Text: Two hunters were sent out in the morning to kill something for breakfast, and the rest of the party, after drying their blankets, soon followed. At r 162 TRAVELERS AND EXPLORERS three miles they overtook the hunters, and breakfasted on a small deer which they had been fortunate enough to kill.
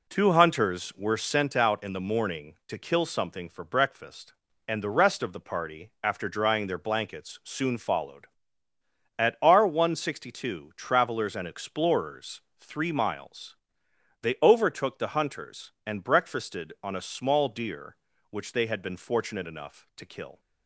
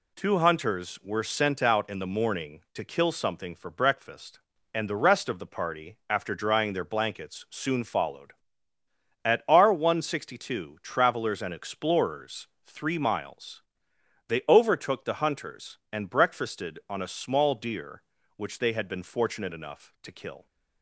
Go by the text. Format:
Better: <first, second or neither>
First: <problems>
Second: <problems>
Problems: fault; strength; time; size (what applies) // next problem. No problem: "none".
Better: second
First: starts louder than the rest; slight; until 1.4 s; 3 dB // pauses between "EXPLORERS" and "three"; slight; at 12.4 s; 0.18 s long // pauses between "miles" and "they"; noticeable; at 13.5 s; 0.66 s long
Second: pauses between "EXPLORERS" and "three"; slight; at 12.4 s; 0.18 s long // pauses between "miles" and "they"; noticeable; at 13.6 s; 0.66 s long